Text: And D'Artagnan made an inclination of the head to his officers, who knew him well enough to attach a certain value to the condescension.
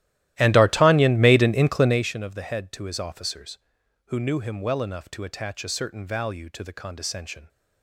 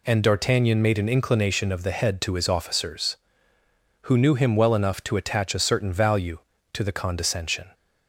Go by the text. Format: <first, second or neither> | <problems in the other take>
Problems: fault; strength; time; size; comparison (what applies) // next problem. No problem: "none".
second | starts louder than the rest; strong; until 2.1 s; 14.5 dB